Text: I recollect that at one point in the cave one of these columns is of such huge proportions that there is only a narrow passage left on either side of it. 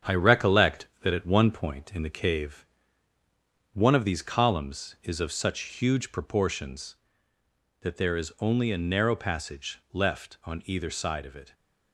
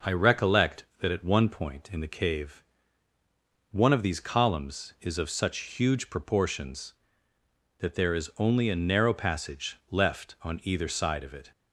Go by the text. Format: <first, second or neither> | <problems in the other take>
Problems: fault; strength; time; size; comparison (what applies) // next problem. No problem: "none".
second | gets quieter; noticeable; throughout; 5 dB // pauses between "cave" and "one"; at 2.6 s; 1.0 s long; also in the second